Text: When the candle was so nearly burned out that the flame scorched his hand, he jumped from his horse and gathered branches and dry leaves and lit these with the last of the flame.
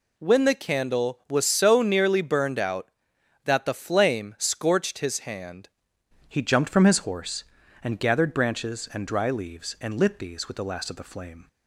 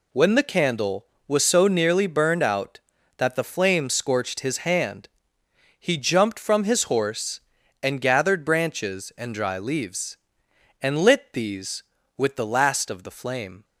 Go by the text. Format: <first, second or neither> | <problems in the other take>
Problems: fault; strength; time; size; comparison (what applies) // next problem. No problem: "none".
second | changes voice at "he"; from 6.2 s on; 5.2 s long